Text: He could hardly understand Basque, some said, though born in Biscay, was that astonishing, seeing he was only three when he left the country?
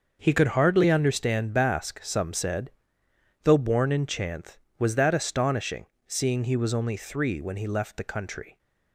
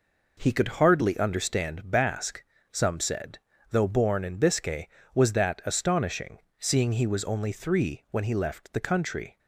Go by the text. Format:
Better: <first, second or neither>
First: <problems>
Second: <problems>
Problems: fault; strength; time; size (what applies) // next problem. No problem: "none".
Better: second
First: starts louder than the rest; until 1.2 s; 6 dB // says "Chanth" for "Biscay"; at 4.0 s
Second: none